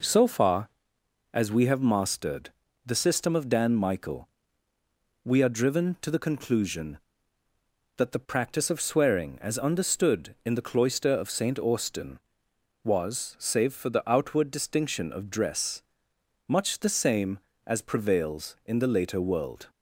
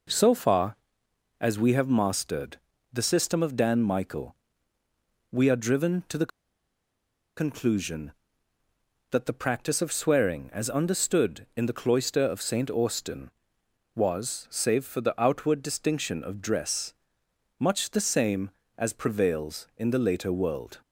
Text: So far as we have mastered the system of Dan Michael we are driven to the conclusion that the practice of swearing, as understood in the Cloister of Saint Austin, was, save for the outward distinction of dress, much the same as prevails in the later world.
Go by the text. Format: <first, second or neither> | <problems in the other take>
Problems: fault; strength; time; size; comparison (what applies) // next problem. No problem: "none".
first | pauses between "mastered" and "the"; slight; at 2.5 s; 0.34 s long; slight in the first // pauses between "Michael" and "we"; noticeable; at 4.3 s; 0.96 s long; noticeable in the first // pauses between "the" and "conclusion"; at 6.3 s; 1.0 s long